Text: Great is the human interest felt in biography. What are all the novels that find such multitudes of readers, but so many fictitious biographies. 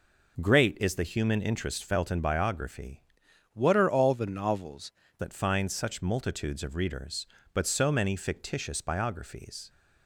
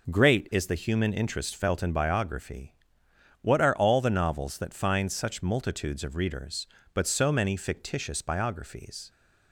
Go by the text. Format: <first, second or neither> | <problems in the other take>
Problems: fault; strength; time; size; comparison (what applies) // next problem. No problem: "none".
second | changes voice from "What" to "novels"; from 3.5 to 4.9 s; 1.4 s long